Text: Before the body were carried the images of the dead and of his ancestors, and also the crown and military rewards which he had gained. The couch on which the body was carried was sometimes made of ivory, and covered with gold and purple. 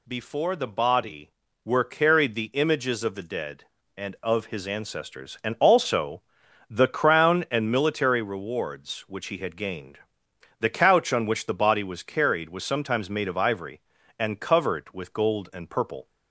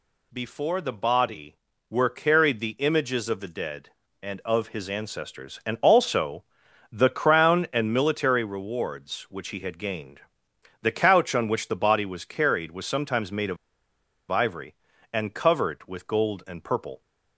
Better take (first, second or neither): first